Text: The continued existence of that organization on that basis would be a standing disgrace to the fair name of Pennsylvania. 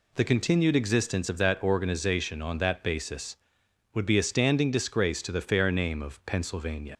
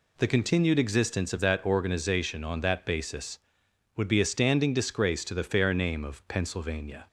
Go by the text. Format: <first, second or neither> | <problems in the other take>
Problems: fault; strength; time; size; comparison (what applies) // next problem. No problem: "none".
second | leaves "Pennsylvania" unfinished; at 6.9 s; 95 ms